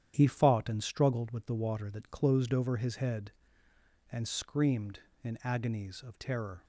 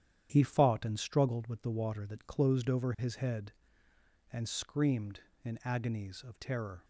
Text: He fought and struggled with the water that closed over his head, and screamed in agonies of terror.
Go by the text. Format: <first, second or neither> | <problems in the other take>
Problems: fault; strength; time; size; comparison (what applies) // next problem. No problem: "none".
neither | starts louder than the rest; strong; the same in both